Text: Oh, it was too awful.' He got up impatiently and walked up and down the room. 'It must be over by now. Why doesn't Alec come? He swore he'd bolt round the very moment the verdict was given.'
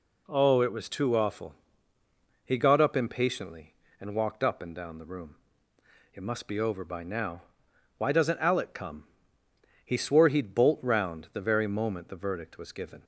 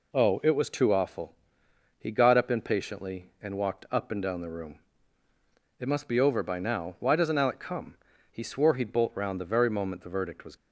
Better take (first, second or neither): first